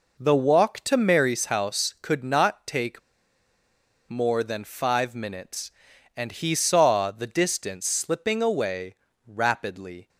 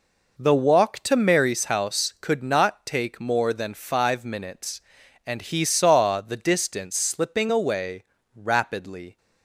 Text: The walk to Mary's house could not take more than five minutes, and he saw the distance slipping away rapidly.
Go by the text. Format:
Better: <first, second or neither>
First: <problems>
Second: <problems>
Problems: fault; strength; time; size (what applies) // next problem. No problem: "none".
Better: second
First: pauses between "take" and "more"; at 3.0 s; 1.0 s long // pauses between "away" and "rapidly"; slight; at 8.9 s; 0.32 s long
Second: pauses between "away" and "rapidly"; slight; at 8.0 s; 0.32 s long